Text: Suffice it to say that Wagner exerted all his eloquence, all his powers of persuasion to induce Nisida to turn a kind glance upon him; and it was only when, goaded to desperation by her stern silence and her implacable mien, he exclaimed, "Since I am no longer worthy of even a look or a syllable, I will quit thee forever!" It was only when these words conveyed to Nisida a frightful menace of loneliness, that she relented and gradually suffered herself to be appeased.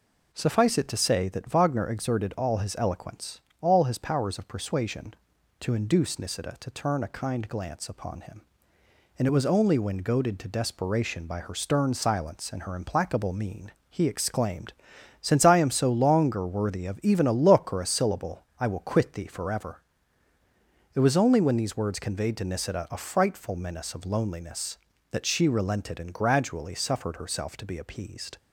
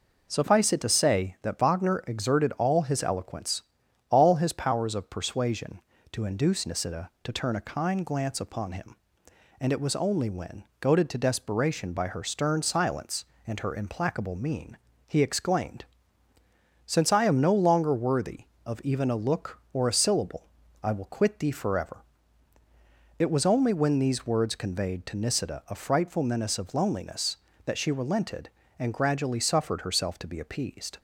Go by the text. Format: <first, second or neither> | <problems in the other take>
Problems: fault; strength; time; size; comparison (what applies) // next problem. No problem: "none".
second | says "so" for "no"; at 15.6 s